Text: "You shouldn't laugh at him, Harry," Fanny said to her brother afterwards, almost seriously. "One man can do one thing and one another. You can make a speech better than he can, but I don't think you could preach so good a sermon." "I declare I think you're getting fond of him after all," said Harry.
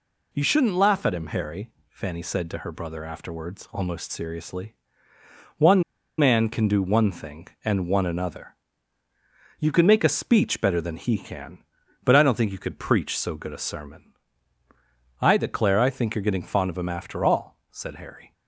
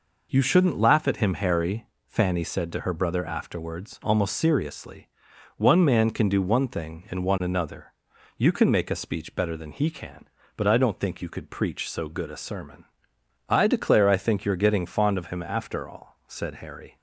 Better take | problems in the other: second | pauses between "One" and "man"; slight; at 5.8 s; 0.35 s long

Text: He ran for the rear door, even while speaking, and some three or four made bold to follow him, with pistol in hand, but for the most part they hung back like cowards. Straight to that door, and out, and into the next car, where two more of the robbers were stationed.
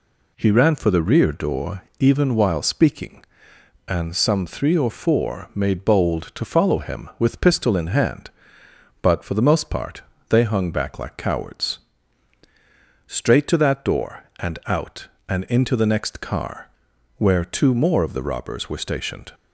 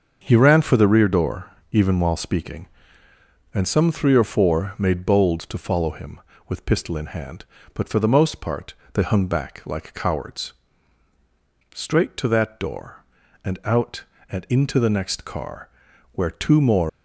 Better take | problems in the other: first | starts louder than the rest; until 1.2 s; 6.5 dB // pauses between "part" and "they"; slight; at 8.7 s; 0.18 s long; slight in the first // stops before "of the robbers were stationed"; at 16.8 s

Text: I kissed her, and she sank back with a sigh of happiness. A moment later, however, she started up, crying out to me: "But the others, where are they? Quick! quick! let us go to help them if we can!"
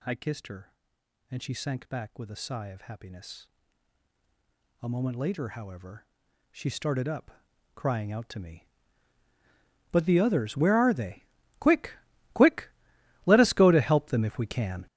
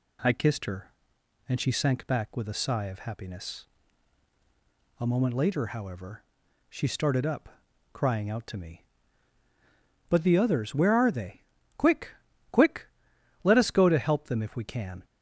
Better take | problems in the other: second | gets louder; strong; throughout; 13 dB

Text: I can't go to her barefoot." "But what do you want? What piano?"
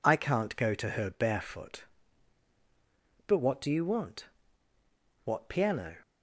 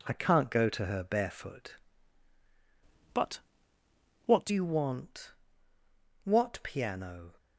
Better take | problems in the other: first | changes voice from "But" to "do"; from 3.1 to 4.5 s; 1.4 s long // pauses between "But" and "what"; noticeable; at 3.3 s; 0.86 s long

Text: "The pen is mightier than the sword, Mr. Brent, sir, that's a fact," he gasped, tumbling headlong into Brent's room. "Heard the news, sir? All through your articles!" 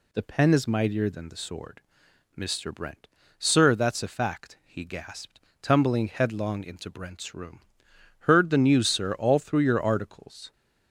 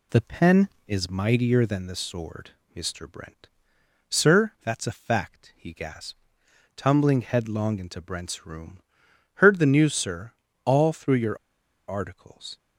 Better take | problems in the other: first | pauses between "your" and "articles"; noticeable; at 11.3 s; 0.52 s long

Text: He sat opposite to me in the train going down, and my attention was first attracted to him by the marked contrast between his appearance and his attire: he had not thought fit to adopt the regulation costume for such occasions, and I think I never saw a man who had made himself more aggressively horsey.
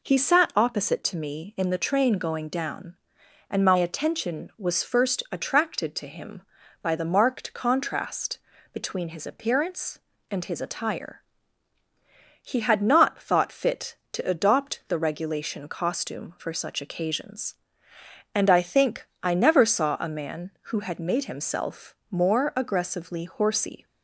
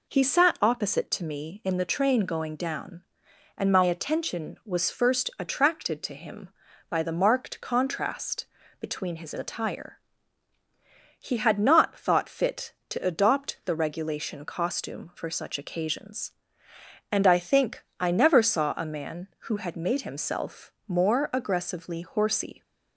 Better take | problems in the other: first | pauses between "contrast" and "between"; slight; at 8.4 s; 0.34 s long; slight in the first // skips "appearance and his"; at 9.3 s // pauses between "think" and "I"; slight; at 17.8 s; 0.16 s long; slight in the first // pauses between "himself" and "more"; slight; at 20.7 s; 0.16 s long; slight in the first

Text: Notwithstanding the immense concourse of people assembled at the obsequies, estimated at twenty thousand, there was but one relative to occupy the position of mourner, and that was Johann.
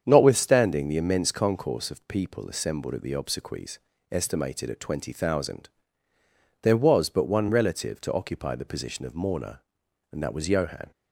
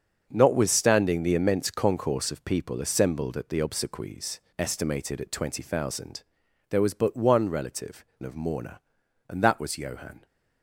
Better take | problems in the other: first | starts louder than the rest; until 1.3 s; 6.5 dB; strong in the first // skips "to occupy the position"; at 8.1 s

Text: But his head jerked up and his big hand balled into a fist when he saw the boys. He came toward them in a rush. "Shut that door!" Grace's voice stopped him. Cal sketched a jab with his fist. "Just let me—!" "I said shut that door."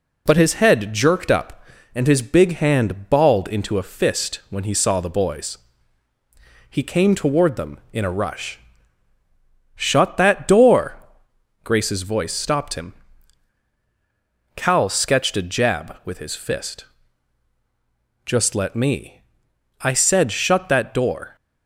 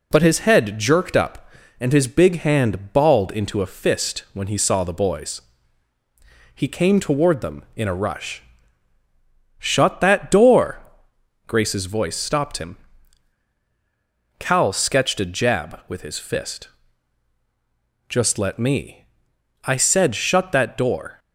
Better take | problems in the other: neither | none

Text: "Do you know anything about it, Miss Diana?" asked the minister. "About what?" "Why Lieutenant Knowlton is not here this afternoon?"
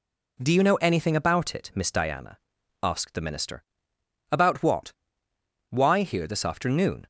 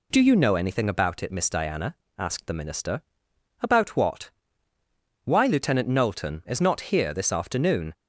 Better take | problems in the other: second | skips "Lieutenant Knowlton is not"; at 6.0 s

